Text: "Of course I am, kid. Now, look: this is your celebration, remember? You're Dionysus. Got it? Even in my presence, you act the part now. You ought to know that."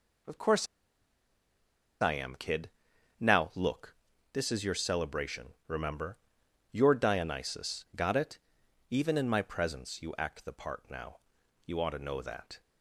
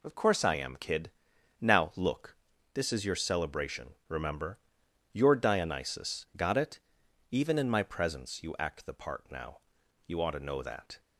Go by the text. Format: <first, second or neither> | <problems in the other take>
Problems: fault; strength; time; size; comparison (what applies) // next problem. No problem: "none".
second | pauses between "course" and "I"; strong; at 0.6 s; 1.3 s long